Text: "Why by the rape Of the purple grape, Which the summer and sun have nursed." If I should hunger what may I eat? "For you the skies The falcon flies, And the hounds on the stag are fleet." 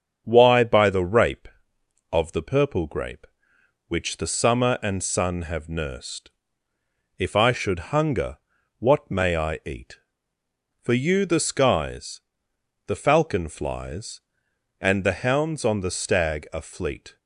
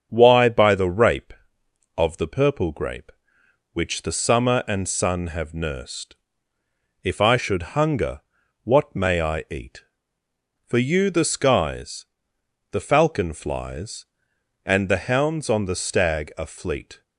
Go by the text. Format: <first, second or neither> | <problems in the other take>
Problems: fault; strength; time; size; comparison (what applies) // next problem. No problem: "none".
neither | starts louder than the rest; strong; the same in both // pauses between "hunger" and "what"; the same in both // pauses between "skies" and "The"; noticeable; the same in both